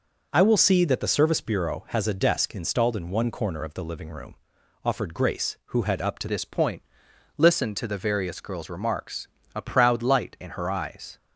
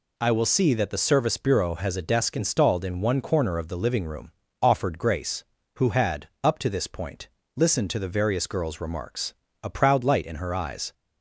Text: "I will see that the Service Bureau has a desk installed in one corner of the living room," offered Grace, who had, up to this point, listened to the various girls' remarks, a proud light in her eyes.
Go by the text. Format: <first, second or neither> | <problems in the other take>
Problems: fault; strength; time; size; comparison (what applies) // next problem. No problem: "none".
second | changes voice at "this"; from 6.2 s on; 4.9 s long